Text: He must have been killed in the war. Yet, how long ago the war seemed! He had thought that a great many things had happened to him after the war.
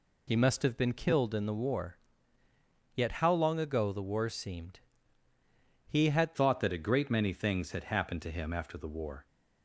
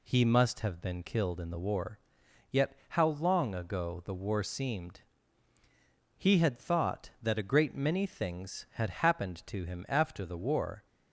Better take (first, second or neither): second